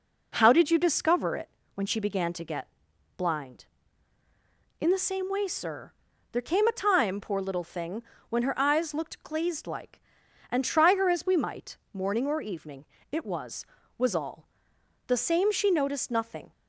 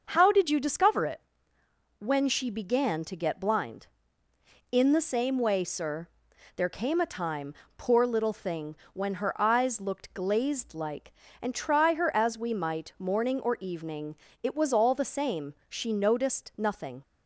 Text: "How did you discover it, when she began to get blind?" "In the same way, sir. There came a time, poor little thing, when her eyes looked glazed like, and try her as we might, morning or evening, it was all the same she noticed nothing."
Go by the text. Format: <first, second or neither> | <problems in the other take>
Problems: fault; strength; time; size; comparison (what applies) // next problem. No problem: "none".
second | pauses between "get" and "blind"; noticeable; at 2.6 s; 0.50 s long // says "was" twice; at 13.9 s // pauses between "all" and "the"; noticeable; at 14.4 s; 0.58 s long